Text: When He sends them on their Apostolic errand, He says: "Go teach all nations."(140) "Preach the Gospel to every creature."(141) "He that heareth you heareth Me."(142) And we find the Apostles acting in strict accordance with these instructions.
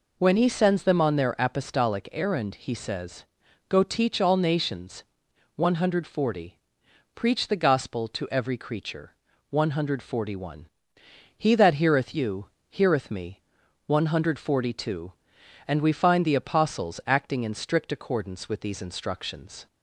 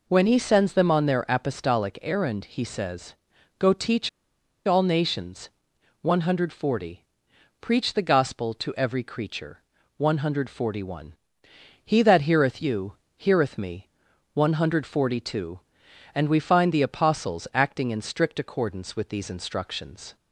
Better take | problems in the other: first | pauses between "teach" and "all"; noticeable; at 4.0 s; 0.56 s long // pauses between "you" and "heareth"; slight; at 12.9 s; 0.24 s long; slight in the first

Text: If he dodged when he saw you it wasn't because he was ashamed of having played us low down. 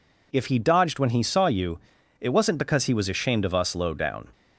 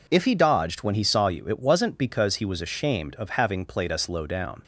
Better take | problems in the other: second | pauses between "you" and "it"; at 1.7 s; 0.42 s long // skips "having played"; at 3.5 s

